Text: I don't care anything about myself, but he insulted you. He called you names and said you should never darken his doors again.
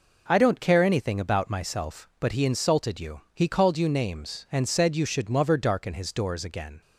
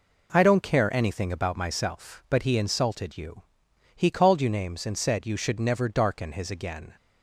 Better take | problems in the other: first | skips "doors"; at 6.4 s

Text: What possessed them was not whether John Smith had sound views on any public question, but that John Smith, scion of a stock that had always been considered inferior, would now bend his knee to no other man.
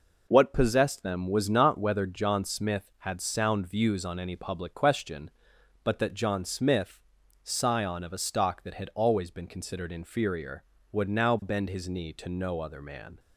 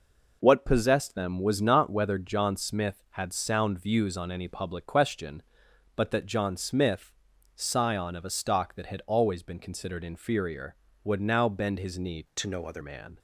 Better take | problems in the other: first | changes voice from "to" to "other"; from 12.3 to 12.8 s; 0.5 s long

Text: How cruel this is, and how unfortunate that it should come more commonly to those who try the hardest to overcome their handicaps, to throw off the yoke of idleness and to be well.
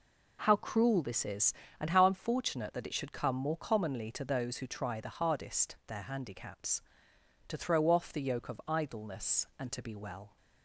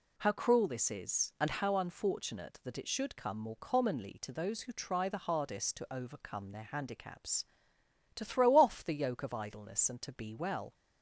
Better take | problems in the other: second | skips "to overcome"; at 5.8 s

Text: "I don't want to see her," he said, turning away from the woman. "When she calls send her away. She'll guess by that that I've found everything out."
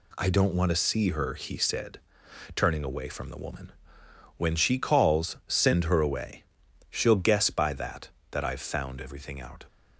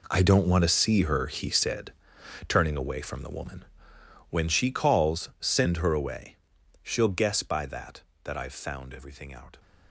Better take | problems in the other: first | gets quieter; strong; throughout; 14 dB

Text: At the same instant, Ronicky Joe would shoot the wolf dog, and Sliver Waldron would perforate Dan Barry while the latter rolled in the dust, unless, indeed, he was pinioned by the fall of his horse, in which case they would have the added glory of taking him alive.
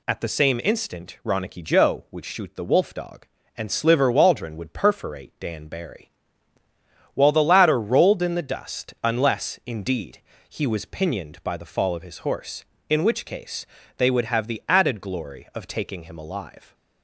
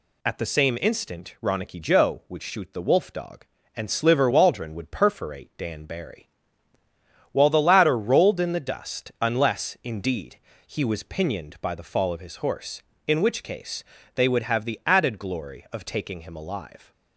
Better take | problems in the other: neither | pauses between "Barry" and "while"; the same in both // pauses between "case" and "they"; slight; the same in both

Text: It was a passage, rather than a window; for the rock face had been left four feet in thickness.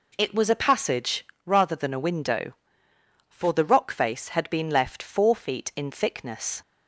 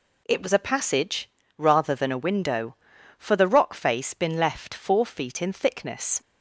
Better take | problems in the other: first | skips "had"; at 4.1 s

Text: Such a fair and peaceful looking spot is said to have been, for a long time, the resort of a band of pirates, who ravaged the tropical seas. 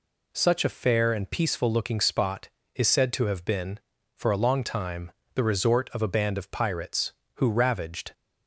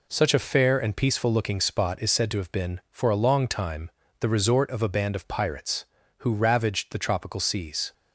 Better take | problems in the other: second | stops before "the tropical seas"; at 8.1 s

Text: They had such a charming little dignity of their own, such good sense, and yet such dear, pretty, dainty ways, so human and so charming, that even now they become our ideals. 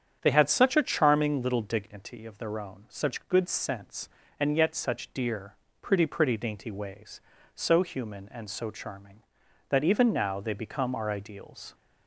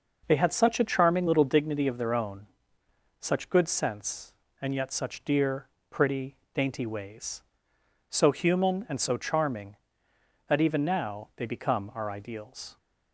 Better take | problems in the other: second | starts louder than the rest; strong; until 1.2 s; 8.5 dB // says "pretty" twice; at 6.0 s

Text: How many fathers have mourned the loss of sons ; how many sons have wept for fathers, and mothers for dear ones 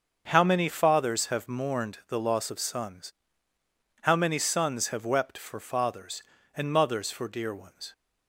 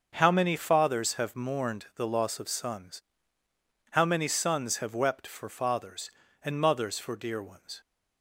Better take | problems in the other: neither | starts louder than the rest; the same in both

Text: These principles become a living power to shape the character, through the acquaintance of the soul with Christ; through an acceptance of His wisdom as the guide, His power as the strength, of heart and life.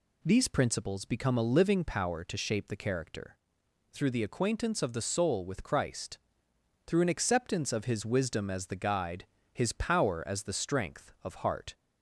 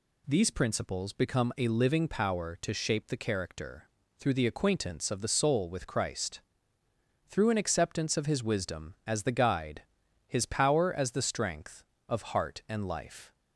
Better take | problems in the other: second | stops before "and life"; at 11.7 s

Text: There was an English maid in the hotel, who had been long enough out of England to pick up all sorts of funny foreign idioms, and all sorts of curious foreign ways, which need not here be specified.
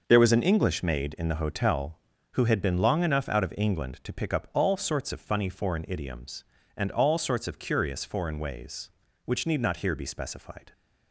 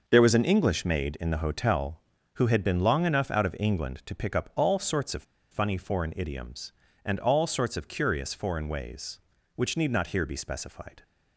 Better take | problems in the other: first | pauses between "of" and "funny"; slight; at 5.2 s; 0.28 s long

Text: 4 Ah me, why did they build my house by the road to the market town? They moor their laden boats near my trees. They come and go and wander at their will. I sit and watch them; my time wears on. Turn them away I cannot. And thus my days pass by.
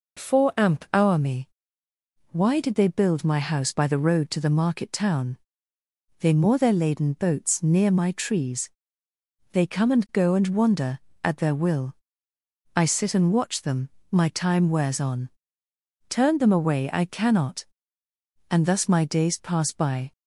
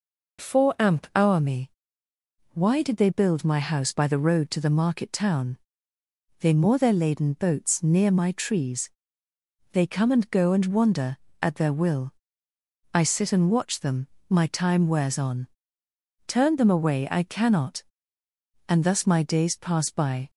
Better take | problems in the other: neither | none

